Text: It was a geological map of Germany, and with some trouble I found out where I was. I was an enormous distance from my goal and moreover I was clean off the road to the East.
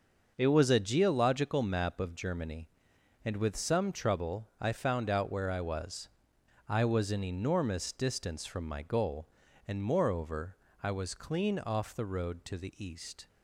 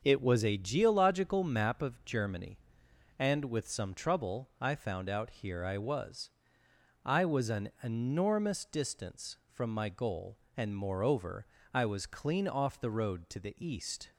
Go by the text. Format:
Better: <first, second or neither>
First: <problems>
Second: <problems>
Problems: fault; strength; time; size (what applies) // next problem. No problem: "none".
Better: first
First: pauses between "moreover" and "I"; slight; at 10.5 s; 0.26 s long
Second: starts louder than the rest; until 1.0 s; 6.5 dB // says "here" for "where"; at 5.3 s // pauses between "moreover" and "I"; slight; at 11.4 s; 0.26 s long